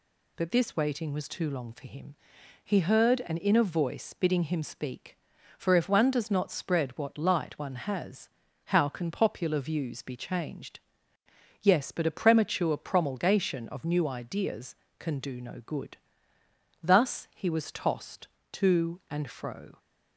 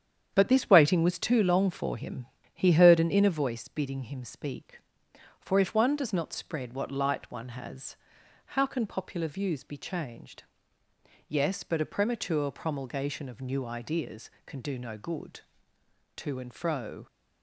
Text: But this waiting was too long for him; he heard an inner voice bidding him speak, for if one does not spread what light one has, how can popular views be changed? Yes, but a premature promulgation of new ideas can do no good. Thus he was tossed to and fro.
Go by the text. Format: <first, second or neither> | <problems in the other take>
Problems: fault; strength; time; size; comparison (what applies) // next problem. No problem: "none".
first | starts louder than the rest; strong; until 1.3 s; 8.5 dB // skips "Thus he was tossed"; at 15.7 s